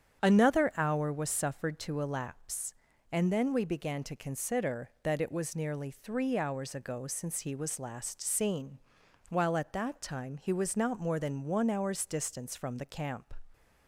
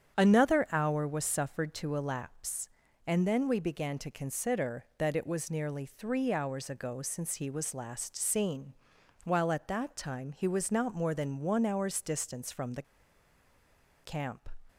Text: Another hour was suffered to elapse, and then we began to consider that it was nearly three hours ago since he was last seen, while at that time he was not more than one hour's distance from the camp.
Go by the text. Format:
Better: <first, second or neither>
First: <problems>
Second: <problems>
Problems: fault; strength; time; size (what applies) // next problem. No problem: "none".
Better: first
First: starts louder than the rest; strong; until 1.2 s; 8.5 dB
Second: starts louder than the rest; strong; until 1.2 s; 8.5 dB // pauses between "the" and "camp"; at 12.8 s; 1.2 s long